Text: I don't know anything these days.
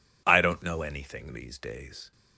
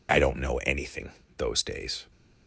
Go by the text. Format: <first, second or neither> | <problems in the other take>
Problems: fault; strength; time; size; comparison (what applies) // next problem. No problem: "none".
first | says "those" for "these"; at 1.3 s